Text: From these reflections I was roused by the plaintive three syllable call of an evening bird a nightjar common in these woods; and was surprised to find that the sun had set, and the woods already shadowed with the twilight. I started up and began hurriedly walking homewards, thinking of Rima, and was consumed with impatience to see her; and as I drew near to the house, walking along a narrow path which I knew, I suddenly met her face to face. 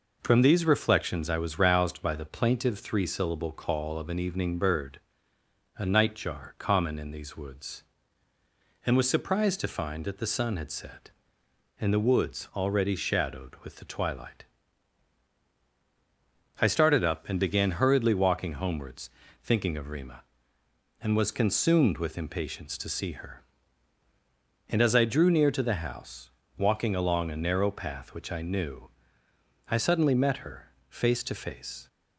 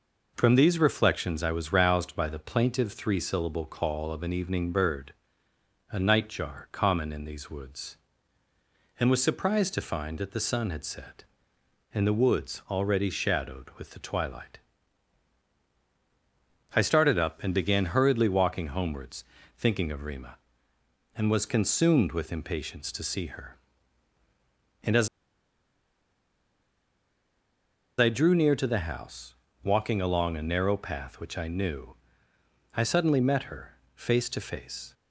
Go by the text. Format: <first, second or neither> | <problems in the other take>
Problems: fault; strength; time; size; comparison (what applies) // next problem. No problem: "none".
first | pauses between "bird" and "a"; noticeable; at 5.1 s; 0.76 s long; noticeable in the first // pauses between "as" and "I"; strong; at 25.0 s; 2.9 s long // pauses between "her" and "face"; slight; at 33.7 s; 0.18 s long; slight in the first